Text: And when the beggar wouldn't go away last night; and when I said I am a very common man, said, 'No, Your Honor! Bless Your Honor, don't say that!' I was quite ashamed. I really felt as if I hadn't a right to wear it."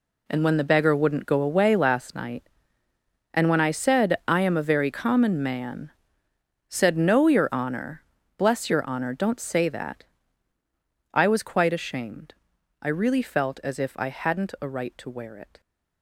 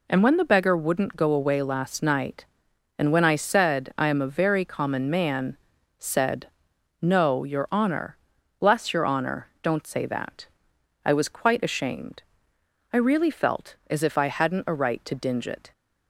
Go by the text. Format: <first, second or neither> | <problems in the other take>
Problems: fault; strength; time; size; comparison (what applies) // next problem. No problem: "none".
first | says "dinge" for "wear"; at 15.1 s